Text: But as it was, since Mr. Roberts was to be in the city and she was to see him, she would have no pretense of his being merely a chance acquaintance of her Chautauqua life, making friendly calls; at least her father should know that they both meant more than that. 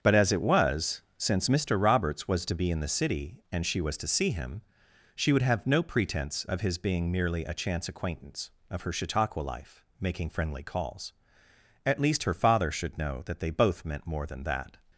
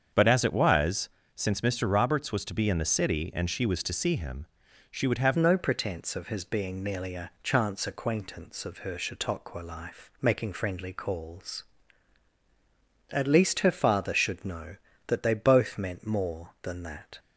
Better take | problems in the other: first | starts louder than the rest; strong; until 1.4 s; 7 dB; strong in the first // changes voice at "no"; from 5.3 s on; 11.8 s long

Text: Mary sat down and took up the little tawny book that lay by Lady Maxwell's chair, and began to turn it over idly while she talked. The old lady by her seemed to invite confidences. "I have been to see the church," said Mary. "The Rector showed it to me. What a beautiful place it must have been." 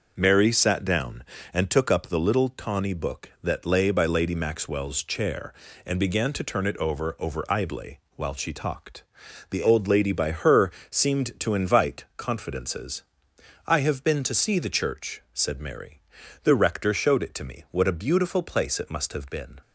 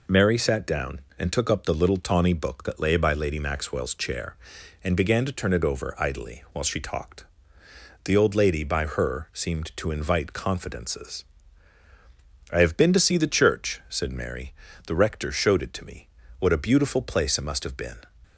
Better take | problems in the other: second | starts louder than the rest; noticeable; until 1.1 s; 6 dB // says "over" twice; at 7.1 s // pauses between "idly" and "while"; slight; at 7.9 s; 0.18 s long // pauses between "her" and "seemed"; slight; at 10.7 s; 0.18 s long

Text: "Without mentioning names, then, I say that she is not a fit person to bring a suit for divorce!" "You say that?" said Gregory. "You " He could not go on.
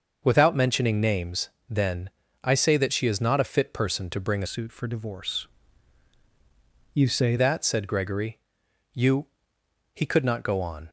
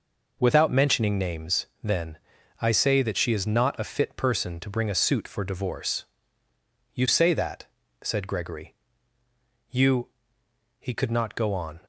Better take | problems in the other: second | starts louder than the rest; until 1.2 s; 6 dB // changes voice from "suit" to "say"; from 4.4 to 7.3 s; 2.9 s long

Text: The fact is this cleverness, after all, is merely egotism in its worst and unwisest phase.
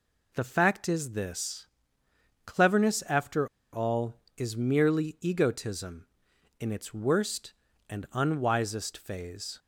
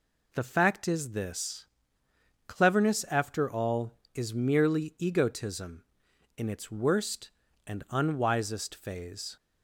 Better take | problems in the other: second | pauses between "this" and "cleverness"; noticeable; at 1.6 s; 0.80 s long; noticeable in the second // pauses between "after" and "all"; slight; at 3.4 s; 0.24 s long

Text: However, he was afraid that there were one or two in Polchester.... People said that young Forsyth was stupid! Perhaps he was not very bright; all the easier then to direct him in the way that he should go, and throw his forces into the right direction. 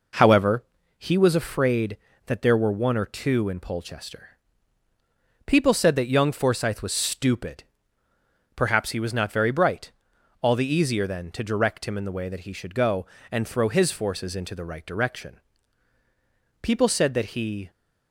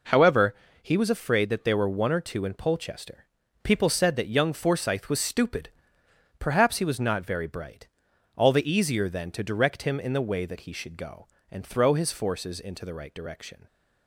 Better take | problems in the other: second | goes on to say "People said that he"; noticeable; from 16.6 s on; 1.0 s long

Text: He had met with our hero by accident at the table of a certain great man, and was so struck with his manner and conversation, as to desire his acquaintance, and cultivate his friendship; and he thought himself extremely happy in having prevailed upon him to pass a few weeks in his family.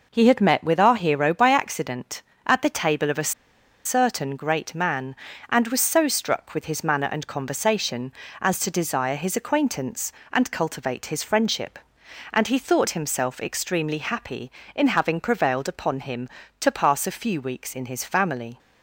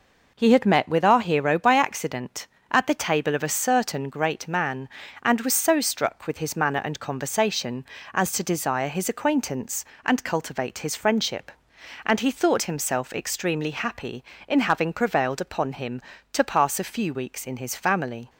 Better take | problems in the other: second | pauses between "a" and "certain"; noticeable; at 3.3 s; 0.54 s long

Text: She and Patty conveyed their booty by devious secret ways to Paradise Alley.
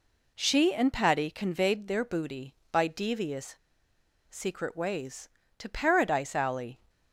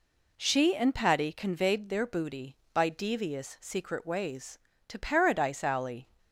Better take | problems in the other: second | pauses between "devious" and "secret"; noticeable; at 3.5 s; 0.76 s long

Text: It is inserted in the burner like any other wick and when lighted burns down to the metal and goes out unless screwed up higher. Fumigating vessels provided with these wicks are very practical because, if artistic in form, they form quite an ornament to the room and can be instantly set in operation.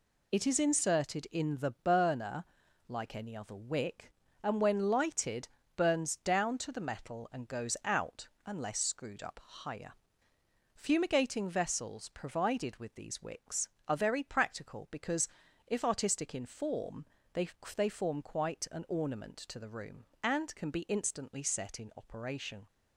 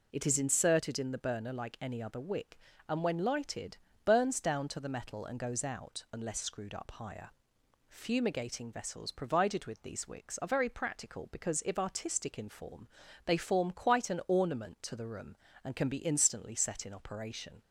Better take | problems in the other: second | pauses between "burner" and "like"; at 2.4 s; 0.42 s long // pauses between "lighted" and "burns"; slight; at 5.4 s; 0.30 s long; slight in the second // pauses between "out" and "unless"; slight; at 8.2 s; 0.16 s long // says "they" twice; at 17.7 s

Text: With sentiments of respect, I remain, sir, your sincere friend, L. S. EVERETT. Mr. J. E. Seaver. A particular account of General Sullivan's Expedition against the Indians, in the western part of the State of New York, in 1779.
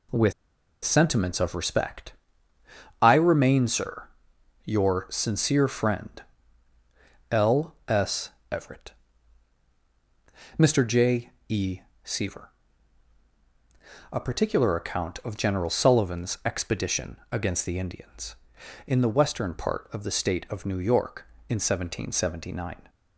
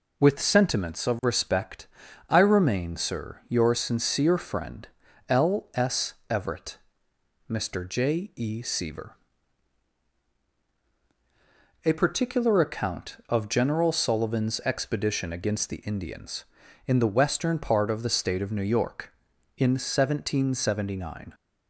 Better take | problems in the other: second | pauses between "With" and "sentiments"; noticeable; at 0.3 s; 0.52 s long // pauses between "S" and "EVERETT"; slight; at 8.3 s; 0.20 s long; slight in the second // pauses between "J" and "E"; slight; at 11.2 s; 0.18 s long // pauses between "E" and "Seaver"; slight; at 11.7 s; 0.24 s long // pauses between "Expedition" and "against"; slight; at 17.1 s; 0.16 s long

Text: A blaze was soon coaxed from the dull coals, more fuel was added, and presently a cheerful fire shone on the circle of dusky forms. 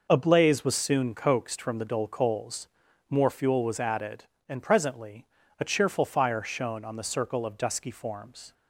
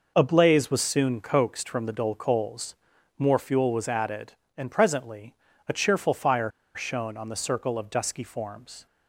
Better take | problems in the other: first | pauses between "presently" and "a"; slight; at 5.3 s; 0.32 s long; slight in the first // pauses between "fire" and "shone"; slight; at 6.4 s; 0.25 s long

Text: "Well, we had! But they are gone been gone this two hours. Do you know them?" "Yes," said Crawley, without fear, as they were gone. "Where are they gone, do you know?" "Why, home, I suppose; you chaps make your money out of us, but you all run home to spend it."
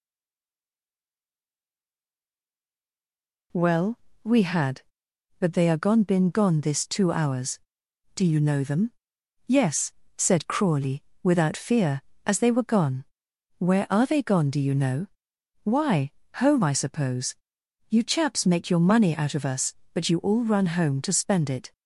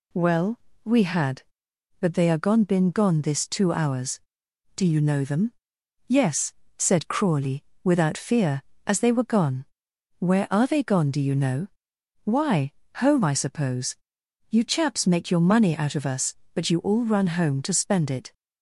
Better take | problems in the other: second | stays silent before the first word; strong; until 3.5 s; 3.5 s long

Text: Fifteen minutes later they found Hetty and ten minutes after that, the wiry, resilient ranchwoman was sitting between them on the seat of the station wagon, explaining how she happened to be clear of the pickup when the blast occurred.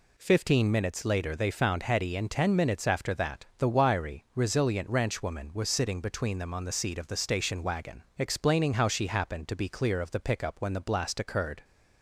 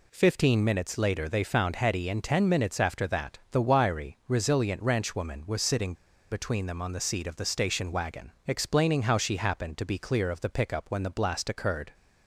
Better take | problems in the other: first | pauses between "sitting" and "between"; at 5.9 s; 0.36 s long

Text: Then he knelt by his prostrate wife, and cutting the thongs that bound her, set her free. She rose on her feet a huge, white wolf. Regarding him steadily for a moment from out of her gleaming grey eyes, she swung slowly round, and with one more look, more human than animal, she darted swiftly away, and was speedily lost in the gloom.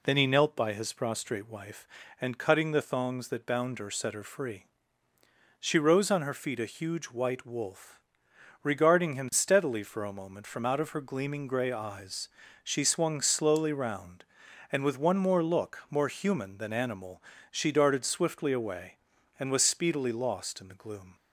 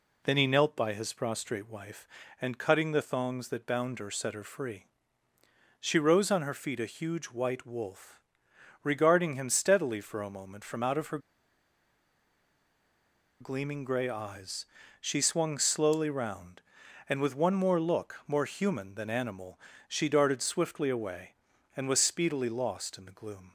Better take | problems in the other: first | pauses between "her" and "gleaming"; strong; at 11.1 s; 2.2 s long

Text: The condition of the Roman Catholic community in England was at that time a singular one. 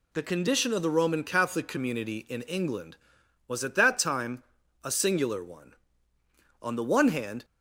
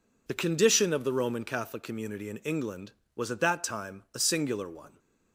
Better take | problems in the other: second | pauses between "time" and "a"; at 4.4 s; 0.40 s long // goes on to say "On the one hand"; noticeable; from 6.6 s on; 0.84 s long

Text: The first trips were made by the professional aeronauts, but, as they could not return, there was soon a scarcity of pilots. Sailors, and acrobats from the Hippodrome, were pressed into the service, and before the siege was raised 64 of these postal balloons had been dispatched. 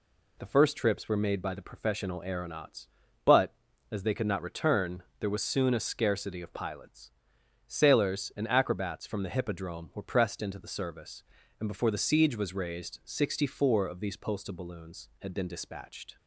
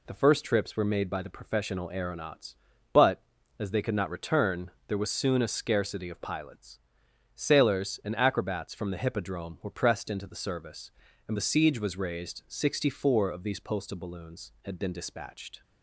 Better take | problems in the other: first | skips "before"; at 11.3 s

